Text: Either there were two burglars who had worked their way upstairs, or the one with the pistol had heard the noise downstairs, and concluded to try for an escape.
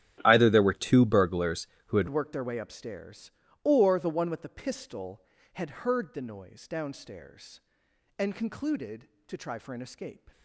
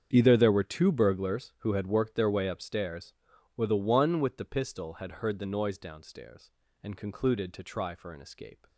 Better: second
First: starts louder than the rest; strong; until 1.2 s; 11.5 dB // changes voice at "worked"; from 2.0 s on; 8.3 s long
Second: starts louder than the rest; strong; until 1.1 s; 7.5 dB

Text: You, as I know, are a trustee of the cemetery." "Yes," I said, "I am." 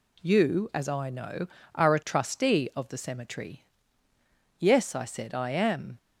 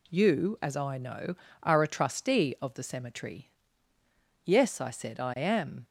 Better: neither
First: none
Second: none

